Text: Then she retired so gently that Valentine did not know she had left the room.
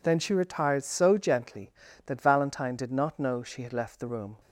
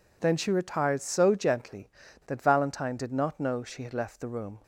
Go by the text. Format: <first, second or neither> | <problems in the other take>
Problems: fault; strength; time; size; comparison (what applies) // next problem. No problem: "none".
neither | none